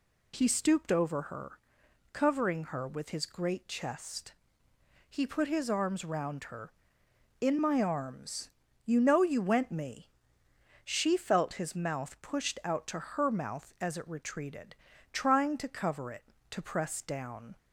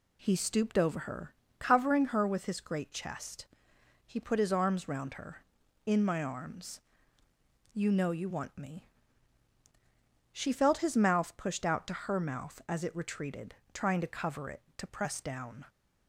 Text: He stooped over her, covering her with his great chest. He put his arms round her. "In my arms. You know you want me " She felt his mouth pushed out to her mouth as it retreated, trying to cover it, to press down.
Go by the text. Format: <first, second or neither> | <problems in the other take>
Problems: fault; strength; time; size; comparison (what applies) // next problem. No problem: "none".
second | says "went" for "want"; at 9.3 s